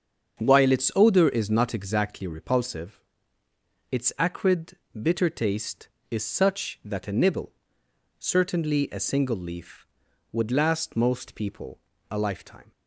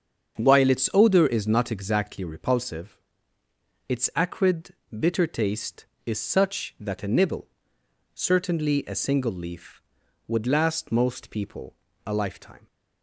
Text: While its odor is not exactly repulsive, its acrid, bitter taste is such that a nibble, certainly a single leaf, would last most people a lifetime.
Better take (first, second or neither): neither